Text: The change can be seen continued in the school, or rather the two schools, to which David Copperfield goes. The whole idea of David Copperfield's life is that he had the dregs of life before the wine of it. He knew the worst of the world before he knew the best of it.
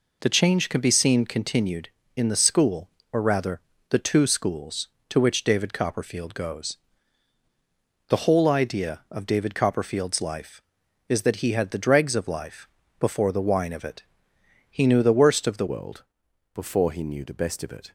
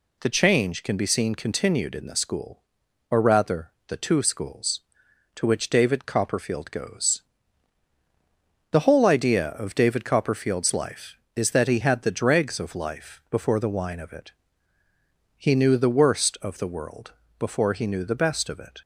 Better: second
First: pauses between "rather" and "the"; slight; at 3.5 s; 0.30 s long // pauses between "life" and "before"; slight; at 12.6 s; 0.32 s long // changes voice at "world"; from 15.6 s on; 2.3 s long // pauses between "world" and "before"; noticeable; at 16.0 s; 0.50 s long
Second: pauses between "rather" and "the"; slight; at 3.6 s; 0.16 s long // pauses between "world" and "before"; slight; at 17.1 s; 0.26 s long

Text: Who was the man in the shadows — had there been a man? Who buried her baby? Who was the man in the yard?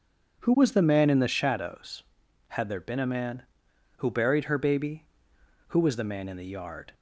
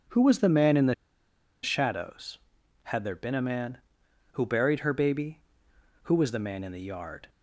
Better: first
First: none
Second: pauses between "the" and "shadows"; noticeable; at 0.9 s; 0.68 s long

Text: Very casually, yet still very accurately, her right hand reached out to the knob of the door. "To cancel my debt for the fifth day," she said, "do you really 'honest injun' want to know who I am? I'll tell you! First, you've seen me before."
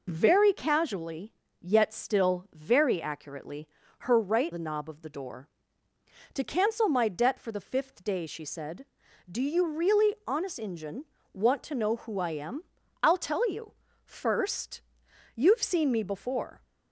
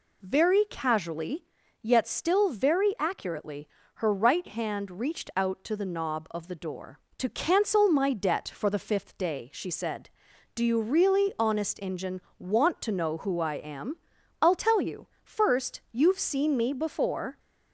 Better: second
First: skips "hand reached out to"; at 4.5 s // pauses between "injun" and "want"; slight; at 11.0 s; 0.26 s long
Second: pauses between "injun" and "want"; slight; at 12.2 s; 0.16 s long

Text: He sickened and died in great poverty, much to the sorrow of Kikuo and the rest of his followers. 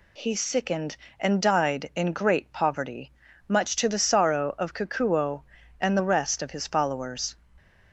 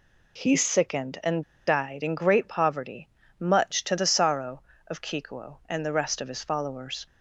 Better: first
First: none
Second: pauses between "and" and "died"; slight; at 1.4 s; 0.24 s long

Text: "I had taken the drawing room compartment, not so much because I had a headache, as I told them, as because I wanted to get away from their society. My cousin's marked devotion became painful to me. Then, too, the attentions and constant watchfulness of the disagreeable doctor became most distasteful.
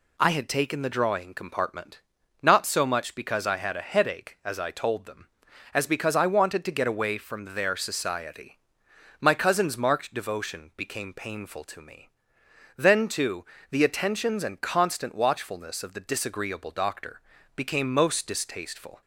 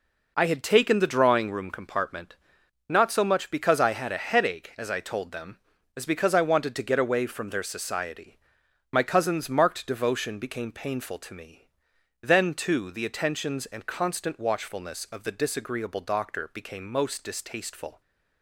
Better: second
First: skips "room"; at 1.3 s // pauses between "doctor" and "became"; slight; at 17.2 s; 0.34 s long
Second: none

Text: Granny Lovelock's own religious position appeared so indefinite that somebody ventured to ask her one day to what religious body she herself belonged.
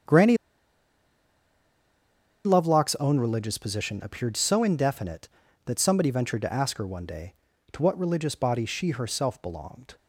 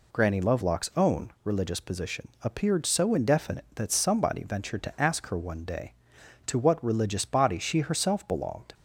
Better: second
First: starts louder than the rest; strong; until 3.1 s; 7.5 dB // pauses between "Granny" and "Lovelock's"; strong; at 0.3 s; 2.0 s long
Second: none

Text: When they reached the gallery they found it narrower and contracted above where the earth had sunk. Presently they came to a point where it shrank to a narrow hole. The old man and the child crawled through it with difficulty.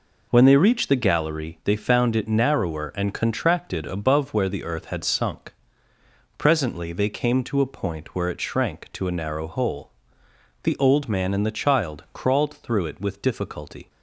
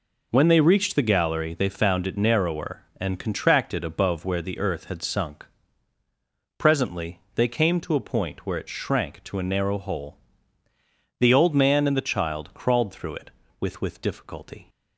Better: first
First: none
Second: pauses between "Presently" and "they"; slight; at 7.1 s; 0.16 s long // says "with" twice; at 13.8 s

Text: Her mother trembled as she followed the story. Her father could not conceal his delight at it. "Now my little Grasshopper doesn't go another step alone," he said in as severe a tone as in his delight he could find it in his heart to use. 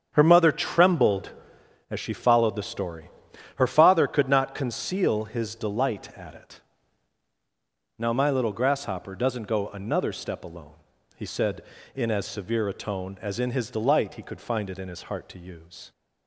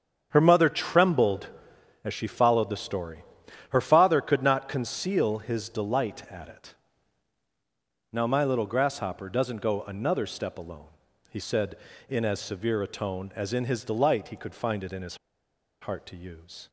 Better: first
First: starts louder than the rest; strong; until 1.1 s; 7.5 dB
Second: starts louder than the rest; strong; until 1.3 s; 7.5 dB // pauses between "his" and "heart"; noticeable; at 15.1 s; 0.64 s long

